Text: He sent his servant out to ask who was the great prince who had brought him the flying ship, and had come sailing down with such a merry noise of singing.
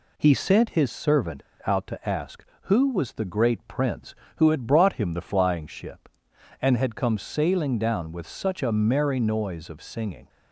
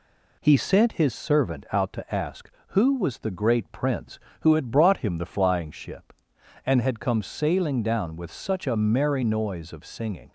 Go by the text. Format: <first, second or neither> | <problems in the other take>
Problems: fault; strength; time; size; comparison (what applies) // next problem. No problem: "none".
second | pauses between "servant" and "out"; slight; at 1.4 s; 0.24 s long